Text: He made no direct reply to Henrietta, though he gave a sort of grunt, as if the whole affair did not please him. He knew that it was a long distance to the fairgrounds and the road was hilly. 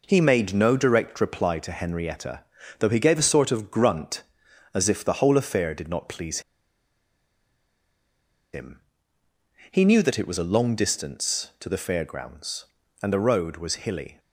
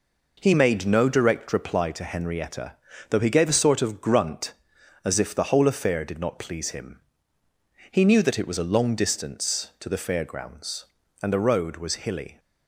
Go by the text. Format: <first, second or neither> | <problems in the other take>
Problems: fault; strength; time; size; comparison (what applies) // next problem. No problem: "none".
second | pauses between "please" and "him"; strong; at 6.4 s; 2.1 s long